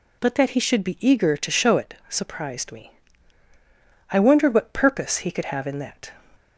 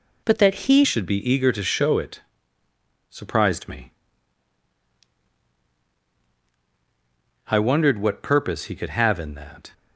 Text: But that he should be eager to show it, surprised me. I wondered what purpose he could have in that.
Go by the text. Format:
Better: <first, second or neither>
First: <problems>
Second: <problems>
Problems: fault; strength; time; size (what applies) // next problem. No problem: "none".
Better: first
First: none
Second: changes voice at "should"; from 0.8 s on; 8.9 s long